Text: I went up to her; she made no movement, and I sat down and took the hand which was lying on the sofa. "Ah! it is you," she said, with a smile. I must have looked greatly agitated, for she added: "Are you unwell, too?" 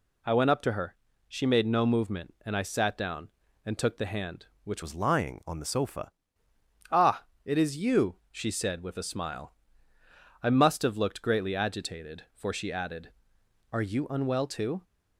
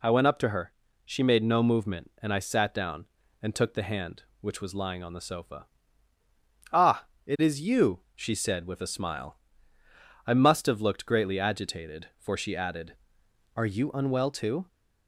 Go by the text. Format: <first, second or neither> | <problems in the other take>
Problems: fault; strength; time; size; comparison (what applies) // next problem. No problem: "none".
second | changes voice from "was" to "sofa"; from 4.8 to 6.1 s; 1.3 s long